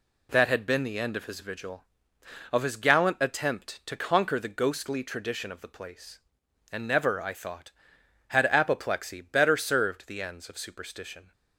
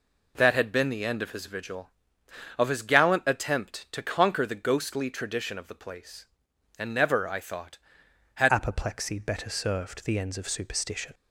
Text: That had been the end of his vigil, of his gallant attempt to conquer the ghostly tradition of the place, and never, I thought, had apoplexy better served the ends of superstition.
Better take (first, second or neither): first